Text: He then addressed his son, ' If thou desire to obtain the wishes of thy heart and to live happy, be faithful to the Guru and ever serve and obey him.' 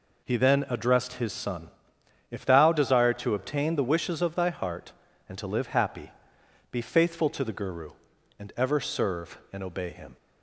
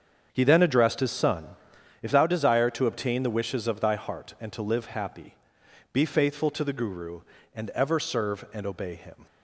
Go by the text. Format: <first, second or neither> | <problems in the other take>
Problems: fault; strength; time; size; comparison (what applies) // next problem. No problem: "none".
first | starts louder than the rest; strong; until 2.0 s; 7 dB